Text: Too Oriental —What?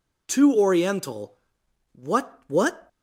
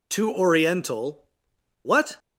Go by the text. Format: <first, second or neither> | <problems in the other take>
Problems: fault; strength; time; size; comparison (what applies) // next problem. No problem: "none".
second | says "What" twice; at 2.4 s